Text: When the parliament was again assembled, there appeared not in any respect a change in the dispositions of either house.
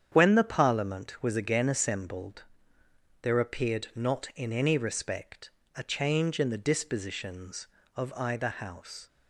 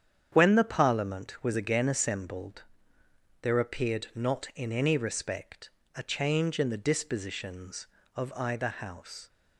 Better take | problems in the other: neither | starts louder than the rest; strong; the same in both // pauses between "respect" and "a"; slight; the same in both

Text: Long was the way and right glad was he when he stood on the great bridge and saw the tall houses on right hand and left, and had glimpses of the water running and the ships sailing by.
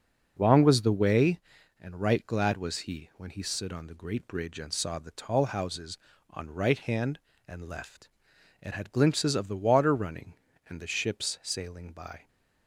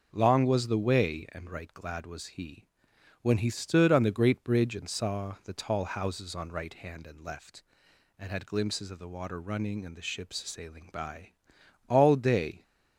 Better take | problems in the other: first | pauses between "he" and "when"; noticeable; at 2.6 s; 0.56 s long // goes on to say "All day"; noticeable; from 11.8 s on; 0.74 s long

